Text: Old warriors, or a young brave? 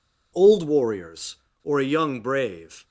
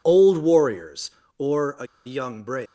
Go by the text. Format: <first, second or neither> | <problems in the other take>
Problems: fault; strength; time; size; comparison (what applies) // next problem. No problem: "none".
first | pauses between "a" and "young"; slight; at 1.8 s; 0.21 s long